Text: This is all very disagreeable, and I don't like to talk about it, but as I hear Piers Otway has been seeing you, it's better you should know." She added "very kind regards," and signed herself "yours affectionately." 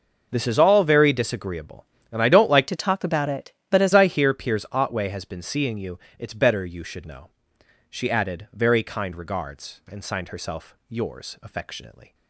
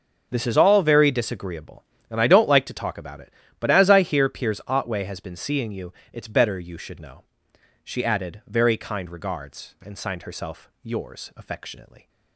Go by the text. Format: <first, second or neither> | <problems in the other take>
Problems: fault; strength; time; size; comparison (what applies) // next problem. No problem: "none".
second | changes voice from "to" to "as"; from 2.6 to 3.9 s; 1.3 s long